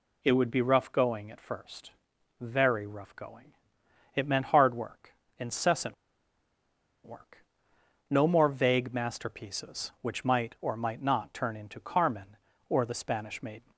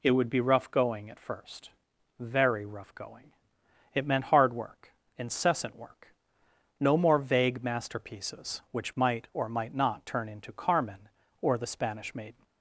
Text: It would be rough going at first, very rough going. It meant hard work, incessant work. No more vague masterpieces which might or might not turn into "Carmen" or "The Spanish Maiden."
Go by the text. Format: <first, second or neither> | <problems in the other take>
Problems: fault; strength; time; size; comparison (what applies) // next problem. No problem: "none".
second | pauses between "incessant" and "work"; at 5.9 s; 1.1 s long